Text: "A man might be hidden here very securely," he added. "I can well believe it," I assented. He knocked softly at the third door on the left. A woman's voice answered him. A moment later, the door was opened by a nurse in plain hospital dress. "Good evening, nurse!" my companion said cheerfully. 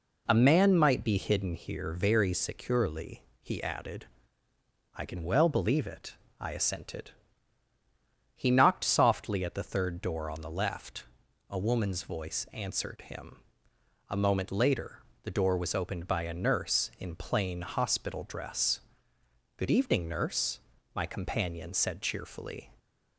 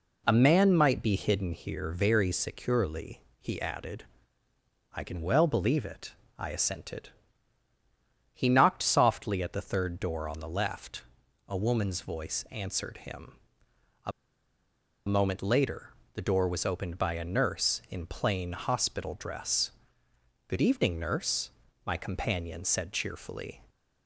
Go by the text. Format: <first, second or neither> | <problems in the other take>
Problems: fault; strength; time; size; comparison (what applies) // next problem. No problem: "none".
first | pauses between "A" and "moment"; noticeable; at 14.1 s; 0.96 s long